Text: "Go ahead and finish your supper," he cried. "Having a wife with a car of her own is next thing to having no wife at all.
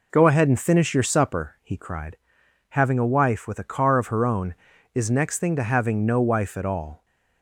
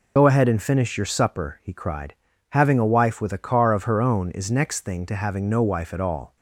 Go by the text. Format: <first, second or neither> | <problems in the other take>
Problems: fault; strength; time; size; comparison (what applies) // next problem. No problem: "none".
first | loses the start of "Go"; at 0.1 s; 80 ms